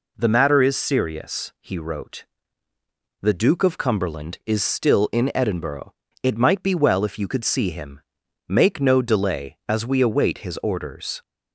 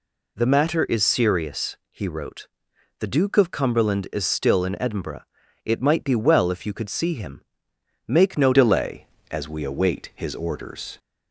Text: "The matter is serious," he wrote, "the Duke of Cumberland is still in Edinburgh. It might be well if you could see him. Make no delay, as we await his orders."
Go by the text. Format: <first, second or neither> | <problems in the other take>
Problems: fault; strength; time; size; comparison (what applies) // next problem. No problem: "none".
first | changes voice at "delay"; from 8.5 s on; 2.4 s long